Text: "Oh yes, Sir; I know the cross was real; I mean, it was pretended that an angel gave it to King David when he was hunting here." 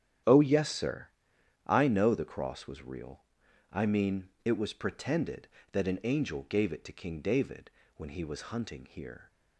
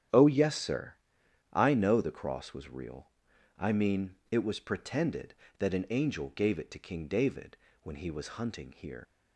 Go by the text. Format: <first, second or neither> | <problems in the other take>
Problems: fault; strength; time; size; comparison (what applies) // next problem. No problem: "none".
first | starts louder than the rest; strong; until 1.7 s; 10 dB; strong in the first // pauses between "David" and "when"; slight; at 7.5 s; 0.28 s long; slight in the first // leaves "here" unfinished; at 9.0 s; 90 ms